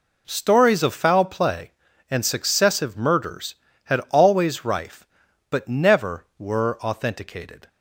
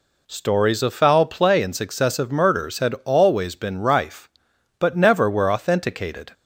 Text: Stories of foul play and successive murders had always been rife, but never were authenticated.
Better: second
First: skips "been"; at 4.6 s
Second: none

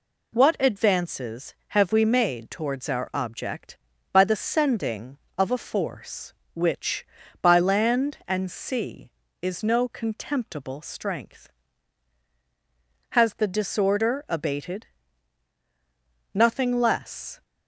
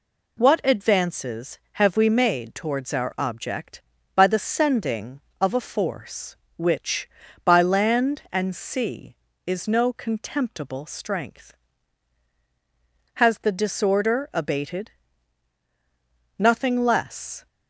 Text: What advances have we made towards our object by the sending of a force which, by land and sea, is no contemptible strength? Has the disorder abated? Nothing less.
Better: neither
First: none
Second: none

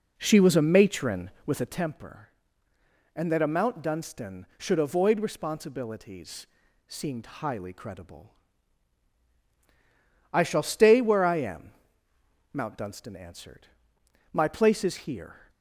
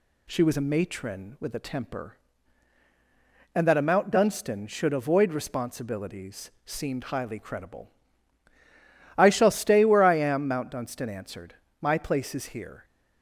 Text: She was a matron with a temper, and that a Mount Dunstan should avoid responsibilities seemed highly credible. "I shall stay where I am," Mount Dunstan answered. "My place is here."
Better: second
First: starts louder than the rest; noticeable; until 1.9 s; 4 dB // pauses between "responsibilities" and "seemed"; at 6.4 s; 0.42 s long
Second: pauses between "responsibilities" and "seemed"; slight; at 6.5 s; 0.16 s long

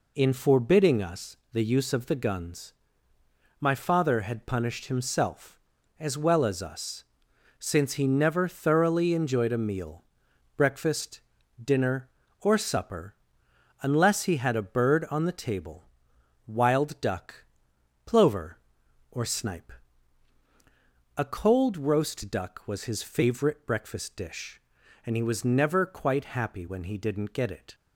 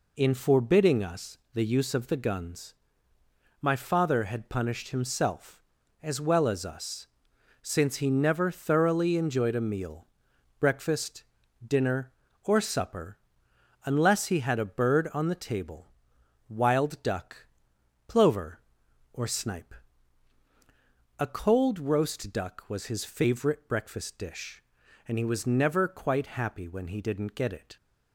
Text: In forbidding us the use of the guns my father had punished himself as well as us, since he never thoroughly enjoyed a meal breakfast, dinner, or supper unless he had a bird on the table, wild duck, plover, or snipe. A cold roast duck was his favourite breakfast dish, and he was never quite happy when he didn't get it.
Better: neither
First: pauses between "us" and "the"; slight; at 1.3 s; 0.16 s long // pauses between "guns" and "my"; noticeable; at 2.7 s; 0.86 s long // pauses between "meal" and "breakfast"; noticeable; at 10.0 s; 0.52 s long // pauses between "supper" and "unless"; noticeable; at 13.1 s; 0.66 s long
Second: pauses between "us" and "the"; slight; at 1.3 s; 0.16 s long // pauses between "guns" and "my"; noticeable; at 2.7 s; 0.86 s long // pauses between "meal" and "breakfast"; noticeable; at 10.0 s; 0.52 s long // pauses between "supper" and "unless"; noticeable; at 13.1 s; 0.66 s long

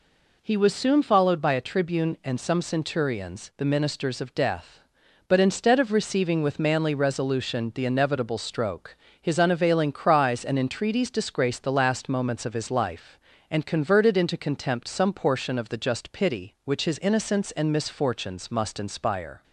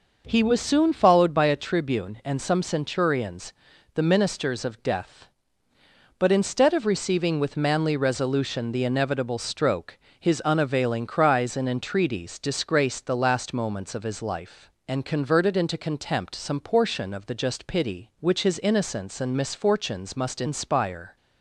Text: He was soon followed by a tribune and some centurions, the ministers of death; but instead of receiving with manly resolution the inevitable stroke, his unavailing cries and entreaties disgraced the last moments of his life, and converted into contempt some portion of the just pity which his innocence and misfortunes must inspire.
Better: neither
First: none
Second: none

